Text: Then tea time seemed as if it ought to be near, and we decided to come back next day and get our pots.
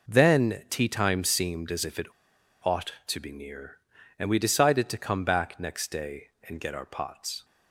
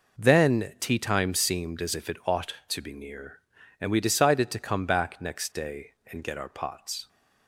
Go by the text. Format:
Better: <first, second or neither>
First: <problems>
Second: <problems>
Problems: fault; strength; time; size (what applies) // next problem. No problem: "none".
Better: second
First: pauses between "it" and "ought"; noticeable; at 2.0 s; 0.58 s long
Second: none